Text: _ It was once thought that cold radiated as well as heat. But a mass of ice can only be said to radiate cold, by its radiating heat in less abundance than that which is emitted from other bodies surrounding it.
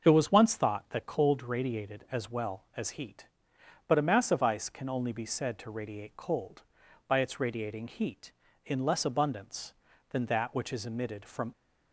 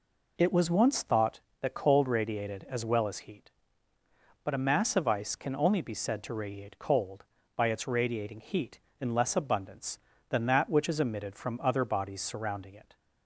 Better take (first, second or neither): second